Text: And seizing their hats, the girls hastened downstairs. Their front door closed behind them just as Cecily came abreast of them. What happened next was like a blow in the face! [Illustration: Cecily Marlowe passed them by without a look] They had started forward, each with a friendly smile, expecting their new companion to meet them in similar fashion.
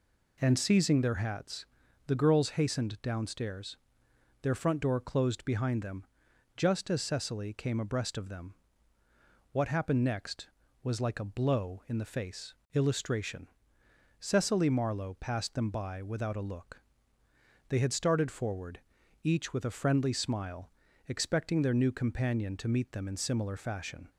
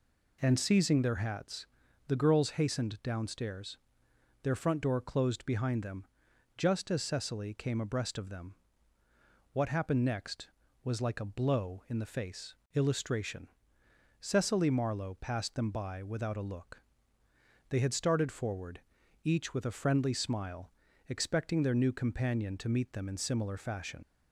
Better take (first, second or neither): first